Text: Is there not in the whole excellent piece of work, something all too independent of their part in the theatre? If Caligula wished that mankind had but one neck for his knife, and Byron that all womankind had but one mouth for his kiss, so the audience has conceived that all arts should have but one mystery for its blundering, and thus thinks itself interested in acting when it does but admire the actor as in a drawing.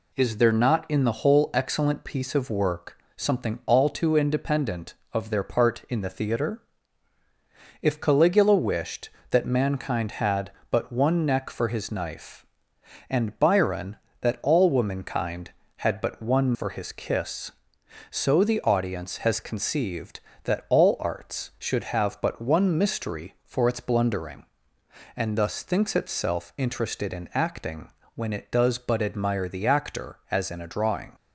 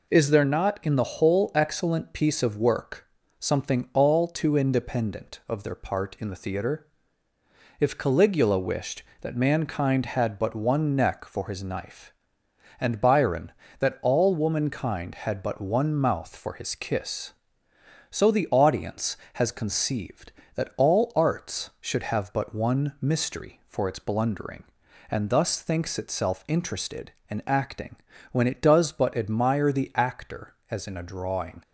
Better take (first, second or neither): second